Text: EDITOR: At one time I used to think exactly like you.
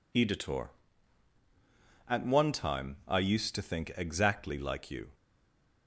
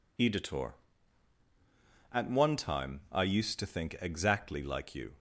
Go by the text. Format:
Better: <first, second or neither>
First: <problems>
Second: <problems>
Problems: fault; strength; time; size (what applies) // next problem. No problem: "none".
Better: second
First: stays silent after the last word; slight; from 5.1 s on; 0.7 s long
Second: none